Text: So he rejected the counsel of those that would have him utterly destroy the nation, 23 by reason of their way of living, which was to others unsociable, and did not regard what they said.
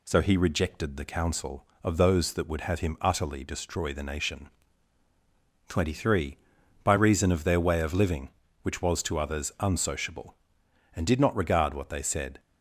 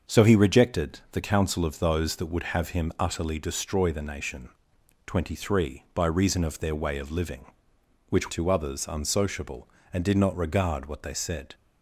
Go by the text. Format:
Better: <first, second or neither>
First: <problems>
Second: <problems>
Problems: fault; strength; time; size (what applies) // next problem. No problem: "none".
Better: first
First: none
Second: starts louder than the rest; until 1.1 s; 6.5 dB // skips "was"; at 8.3 s